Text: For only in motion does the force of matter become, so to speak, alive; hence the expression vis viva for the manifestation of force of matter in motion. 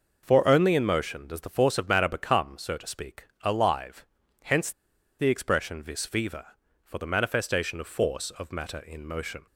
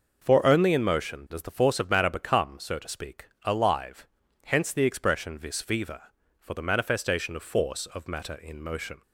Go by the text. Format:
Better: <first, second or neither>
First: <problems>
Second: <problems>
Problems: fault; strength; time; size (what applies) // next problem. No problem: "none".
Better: second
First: pauses between "hence" and "the"; noticeable; at 4.7 s; 0.48 s long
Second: none